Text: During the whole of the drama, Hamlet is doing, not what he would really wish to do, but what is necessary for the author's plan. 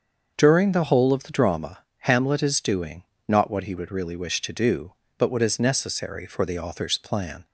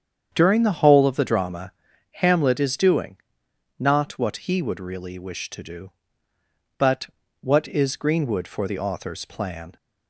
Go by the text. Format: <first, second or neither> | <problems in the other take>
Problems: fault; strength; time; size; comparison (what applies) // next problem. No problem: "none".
first | starts louder than the rest; strong; until 1.3 s; 8 dB; also in the first // pauses between "but" and "what"; slight; at 7.0 s; 0.34 s long // says "greenwood" for "necessary"; at 7.9 s